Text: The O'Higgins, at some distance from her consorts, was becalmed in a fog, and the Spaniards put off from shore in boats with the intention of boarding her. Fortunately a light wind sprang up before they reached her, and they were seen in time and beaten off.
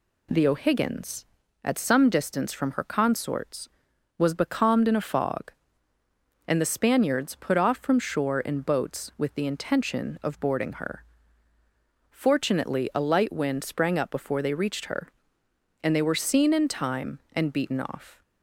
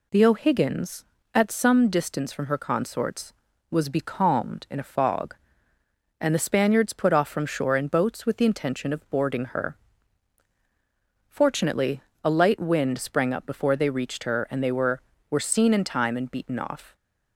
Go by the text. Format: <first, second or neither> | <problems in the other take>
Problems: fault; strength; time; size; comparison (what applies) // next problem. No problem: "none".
first | pauses between "Fortunately" and "a"; slight; at 12.0 s; 0.22 s long // says "were" twice; at 15.2 s